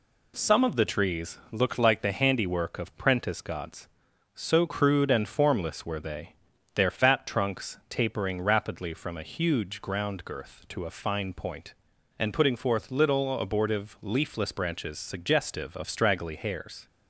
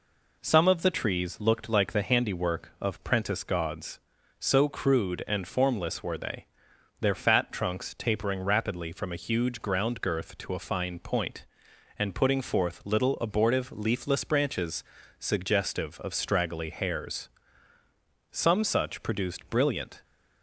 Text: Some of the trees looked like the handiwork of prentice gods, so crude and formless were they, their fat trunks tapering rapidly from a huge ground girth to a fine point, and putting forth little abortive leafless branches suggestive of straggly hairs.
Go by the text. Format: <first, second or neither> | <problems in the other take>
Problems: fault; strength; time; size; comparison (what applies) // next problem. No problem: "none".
first | pauses between "branches" and "suggestive"; slight; at 14.8 s; 0.34 s long // goes on to say "Some such produced brilliant"; strong; from 18.3 s on; 1.7 s long